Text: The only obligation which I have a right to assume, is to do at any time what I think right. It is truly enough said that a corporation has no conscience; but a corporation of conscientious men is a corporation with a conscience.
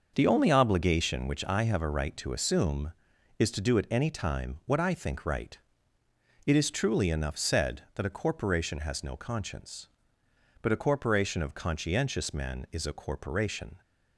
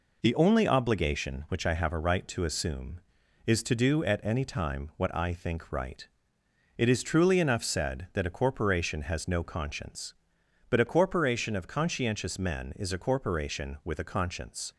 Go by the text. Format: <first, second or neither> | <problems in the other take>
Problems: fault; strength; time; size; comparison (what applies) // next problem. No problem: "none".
second | starts louder than the rest; until 1.1 s; 6.5 dB // stops before "with a conscience"; at 13.8 s